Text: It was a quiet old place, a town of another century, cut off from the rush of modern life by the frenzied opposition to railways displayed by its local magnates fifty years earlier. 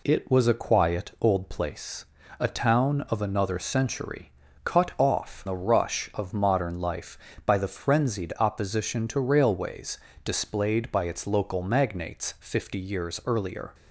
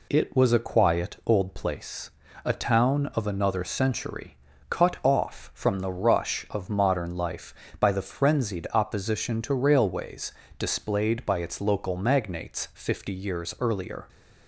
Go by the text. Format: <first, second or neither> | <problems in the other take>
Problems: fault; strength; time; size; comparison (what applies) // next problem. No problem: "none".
second | skips "from"; at 5.4 s // pauses between "railways" and "displayed"; slight; at 9.9 s; 0.26 s long; slight in the second